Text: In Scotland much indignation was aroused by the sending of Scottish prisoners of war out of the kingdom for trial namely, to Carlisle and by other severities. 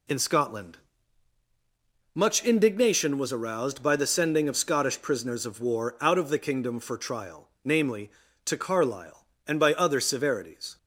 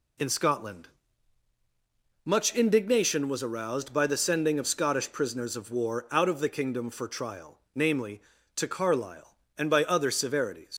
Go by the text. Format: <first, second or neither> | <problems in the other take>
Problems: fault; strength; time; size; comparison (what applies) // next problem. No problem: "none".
first | pauses between "Scotland" and "much"; strong; at 0.8 s; 1.3 s long; strong in the first // leaves "severities" unfinished; at 10.7 s; 105 ms